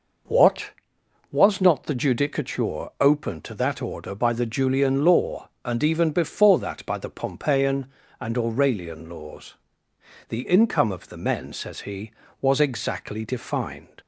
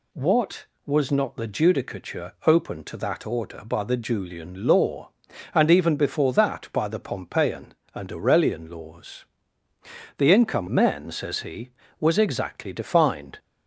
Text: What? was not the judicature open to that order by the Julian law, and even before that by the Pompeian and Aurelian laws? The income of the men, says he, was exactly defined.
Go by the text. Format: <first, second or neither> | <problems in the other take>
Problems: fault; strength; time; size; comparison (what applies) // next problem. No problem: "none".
first | skips "of the"; at 10.6 s